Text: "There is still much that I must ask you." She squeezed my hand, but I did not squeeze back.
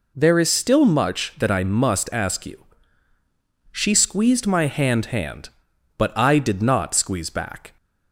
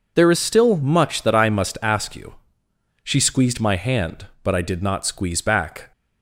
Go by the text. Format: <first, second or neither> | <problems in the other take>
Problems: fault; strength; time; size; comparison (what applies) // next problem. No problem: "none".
second | says "hand" twice; at 5.0 s